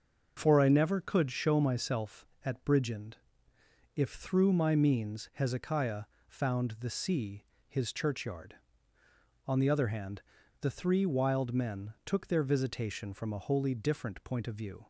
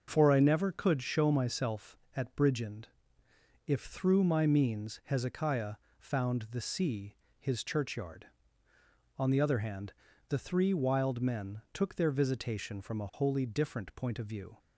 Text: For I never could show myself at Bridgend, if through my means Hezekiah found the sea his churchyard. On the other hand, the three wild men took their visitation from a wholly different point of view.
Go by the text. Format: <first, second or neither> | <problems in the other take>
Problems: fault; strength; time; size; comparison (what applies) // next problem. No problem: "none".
neither | starts louder than the rest; noticeable; the same in both // pauses between "Hezekiah" and "found"; slight; the same in both // pauses between "sea" and "his"; slight; the same in both